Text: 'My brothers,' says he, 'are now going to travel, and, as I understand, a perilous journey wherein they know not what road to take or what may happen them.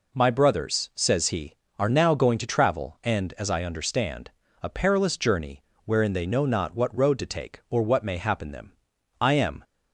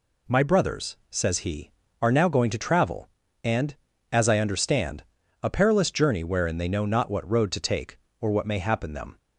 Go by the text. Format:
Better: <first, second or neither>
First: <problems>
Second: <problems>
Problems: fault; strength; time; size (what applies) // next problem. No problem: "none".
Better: second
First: pauses between "journey" and "wherein"; slight; at 5.6 s; 0.22 s long // goes on to say "I am"; slight; from 9.2 s on; 0.42 s long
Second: none